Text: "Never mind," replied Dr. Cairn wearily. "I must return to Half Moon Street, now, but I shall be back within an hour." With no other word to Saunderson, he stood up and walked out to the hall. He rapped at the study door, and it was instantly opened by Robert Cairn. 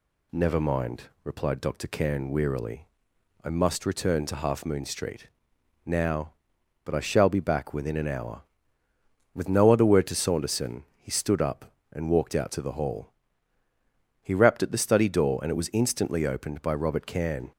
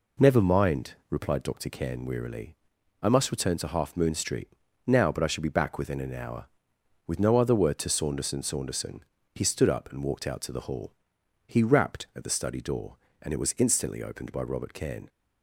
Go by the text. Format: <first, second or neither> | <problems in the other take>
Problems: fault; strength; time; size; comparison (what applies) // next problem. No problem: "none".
first | says "Saunderson" twice; at 8.4 s